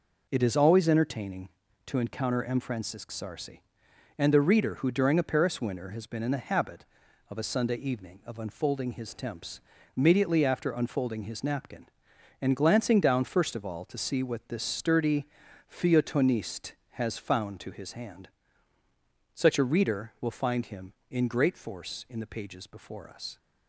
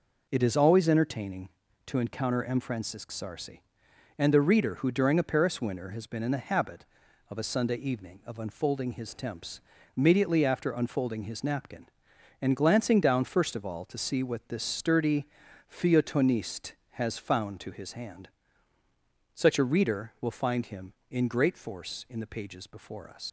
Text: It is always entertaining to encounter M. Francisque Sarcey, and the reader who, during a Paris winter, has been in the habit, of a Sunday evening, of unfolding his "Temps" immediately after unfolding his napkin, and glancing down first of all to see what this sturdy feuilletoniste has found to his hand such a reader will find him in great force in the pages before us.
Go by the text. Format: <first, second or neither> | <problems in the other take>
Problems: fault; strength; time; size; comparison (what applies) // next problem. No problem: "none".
first | pauses between "Temps" and "immediately"; at 9.5 s; 0.38 s long; also in the first // pauses between "sturdy" and "feuilletoniste"; at 15.2 s; 0.44 s long; also in the first // pauses between "hand" and "such"; at 18.2 s; 1.0 s long; also in the first // leaves "us" unfinished; at 23.2 s; 75 ms